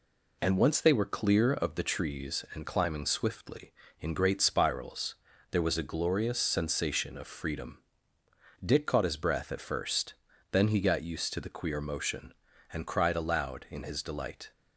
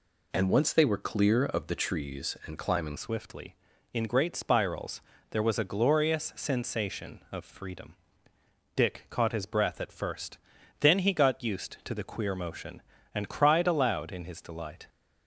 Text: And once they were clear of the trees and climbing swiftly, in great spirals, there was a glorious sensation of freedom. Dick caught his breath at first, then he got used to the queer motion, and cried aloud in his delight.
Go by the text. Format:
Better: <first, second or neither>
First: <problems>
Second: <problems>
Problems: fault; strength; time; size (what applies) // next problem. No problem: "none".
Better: first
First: none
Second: changes voice at "swiftly"; from 2.9 s on; 11.9 s long